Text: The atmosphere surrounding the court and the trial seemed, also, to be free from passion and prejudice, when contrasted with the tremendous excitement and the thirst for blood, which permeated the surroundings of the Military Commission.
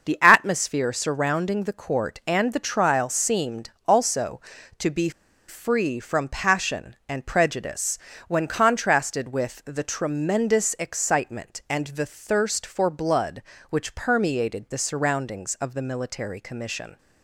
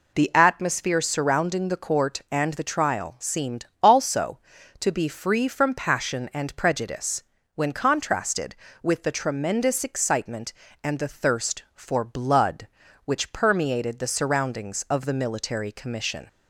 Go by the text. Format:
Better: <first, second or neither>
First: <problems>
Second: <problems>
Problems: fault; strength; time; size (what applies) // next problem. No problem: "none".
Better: second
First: starts louder than the rest; until 1.1 s; 6.5 dB // pauses between "be" and "free"; at 5.0 s; 0.38 s long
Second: none